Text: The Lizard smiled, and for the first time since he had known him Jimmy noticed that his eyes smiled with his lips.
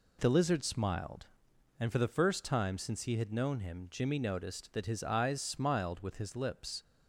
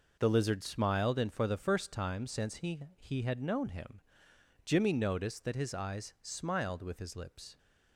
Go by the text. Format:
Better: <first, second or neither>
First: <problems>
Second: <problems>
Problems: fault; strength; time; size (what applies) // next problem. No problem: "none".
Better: first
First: none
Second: says "he" twice; at 2.9 s // pauses between "him" and "Jimmy"; noticeable; at 4.0 s; 0.64 s long